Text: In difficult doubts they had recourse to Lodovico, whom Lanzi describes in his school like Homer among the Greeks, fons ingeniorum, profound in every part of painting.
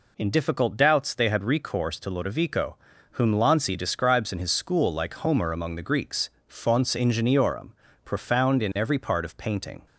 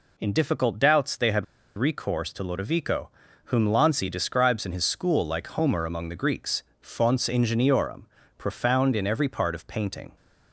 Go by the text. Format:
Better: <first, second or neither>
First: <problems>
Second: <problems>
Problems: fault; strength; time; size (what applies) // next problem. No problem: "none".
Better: first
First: none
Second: pauses between "had" and "recourse"; slight; at 1.4 s; 0.32 s long